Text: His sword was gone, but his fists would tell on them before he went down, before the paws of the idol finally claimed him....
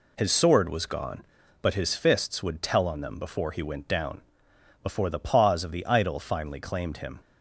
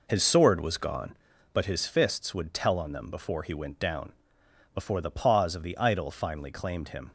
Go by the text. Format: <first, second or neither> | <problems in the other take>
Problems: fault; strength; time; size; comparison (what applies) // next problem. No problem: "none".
first | starts louder than the rest; noticeable; until 1.1 s; 4.5 dB